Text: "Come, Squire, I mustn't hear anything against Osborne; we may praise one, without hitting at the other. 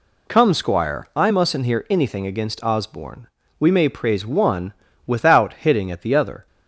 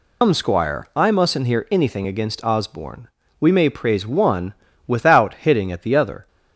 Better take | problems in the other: first | loses the start of "Come"; at 0.2 s; 140 ms

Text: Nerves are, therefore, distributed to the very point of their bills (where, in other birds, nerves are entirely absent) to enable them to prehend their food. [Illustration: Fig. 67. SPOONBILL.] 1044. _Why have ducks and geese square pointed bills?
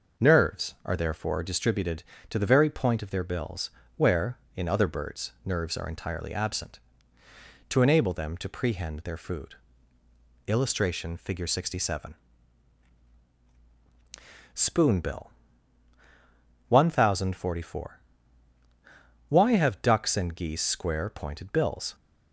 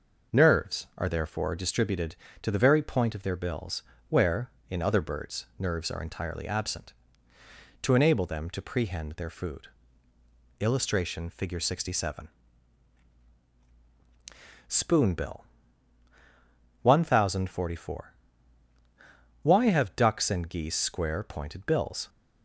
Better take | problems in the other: neither | none

